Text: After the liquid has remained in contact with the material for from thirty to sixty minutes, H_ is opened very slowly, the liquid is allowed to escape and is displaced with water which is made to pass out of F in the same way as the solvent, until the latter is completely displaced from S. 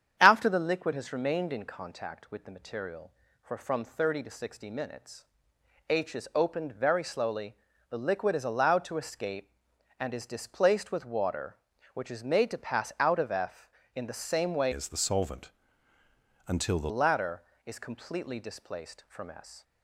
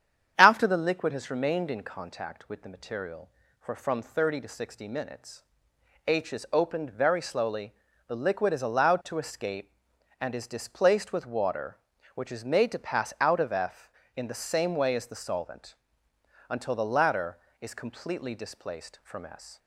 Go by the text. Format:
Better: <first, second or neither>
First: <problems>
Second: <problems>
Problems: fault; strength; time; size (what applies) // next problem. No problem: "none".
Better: second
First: starts louder than the rest; strong; until 1.2 s; 8.5 dB // changes voice from "as" to "the"; from 14.7 to 16.9 s; 2.2 s long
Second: starts louder than the rest; strong; until 1.3 s; 8.5 dB